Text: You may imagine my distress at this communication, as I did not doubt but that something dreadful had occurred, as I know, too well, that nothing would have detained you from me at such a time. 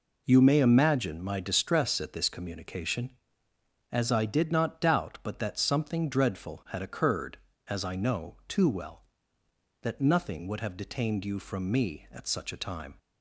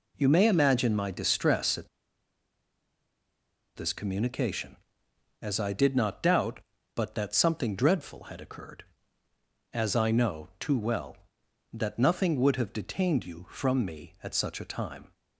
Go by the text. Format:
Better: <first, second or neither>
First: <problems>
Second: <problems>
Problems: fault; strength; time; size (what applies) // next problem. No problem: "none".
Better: first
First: none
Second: pauses between "at" and "this"; strong; at 1.8 s; 1.8 s long